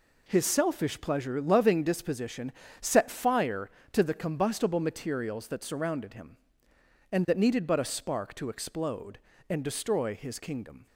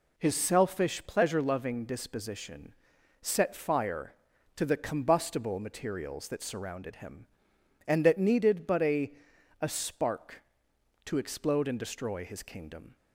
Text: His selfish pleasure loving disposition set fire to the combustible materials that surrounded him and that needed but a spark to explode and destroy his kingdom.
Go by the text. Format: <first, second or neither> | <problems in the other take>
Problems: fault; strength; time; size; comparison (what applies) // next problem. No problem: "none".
first | pauses between "disposition" and "set"; noticeable; at 2.7 s; 0.48 s long; slight in the first // says "a" twice; at 9.5 s